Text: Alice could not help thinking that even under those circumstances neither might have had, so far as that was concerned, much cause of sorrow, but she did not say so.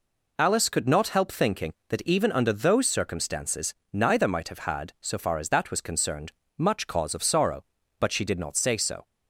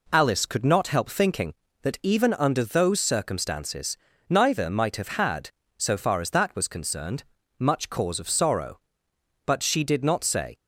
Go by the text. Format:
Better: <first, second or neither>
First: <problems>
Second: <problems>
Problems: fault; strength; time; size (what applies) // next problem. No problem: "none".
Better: first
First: pauses between "circumstances" and "neither"; slight; at 3.7 s; 0.20 s long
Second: pauses between "circumstances" and "neither"; slight; at 3.9 s; 0.32 s long // stops before "so"; at 10.5 s